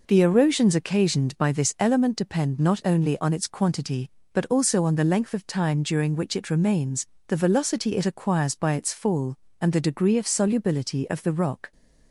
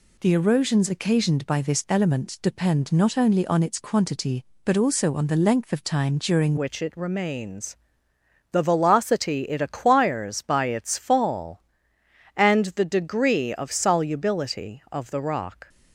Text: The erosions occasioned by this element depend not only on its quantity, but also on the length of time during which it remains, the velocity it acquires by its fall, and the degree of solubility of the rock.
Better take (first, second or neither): first